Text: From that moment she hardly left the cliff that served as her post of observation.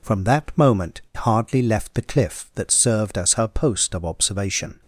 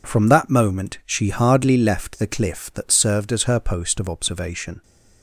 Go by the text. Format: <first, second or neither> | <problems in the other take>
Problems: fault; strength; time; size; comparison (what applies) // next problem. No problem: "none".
second | skips "she"; at 1.0 s